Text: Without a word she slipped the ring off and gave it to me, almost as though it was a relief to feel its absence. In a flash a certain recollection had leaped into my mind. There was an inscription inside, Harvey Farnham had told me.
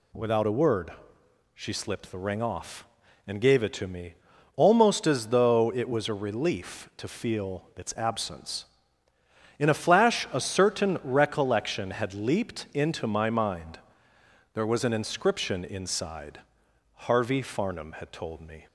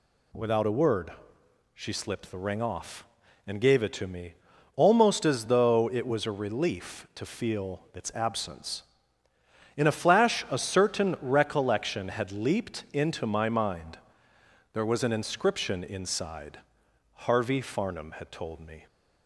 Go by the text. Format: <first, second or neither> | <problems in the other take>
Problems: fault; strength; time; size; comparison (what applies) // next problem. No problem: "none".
neither | pauses between "word" and "she"; noticeable; the same in both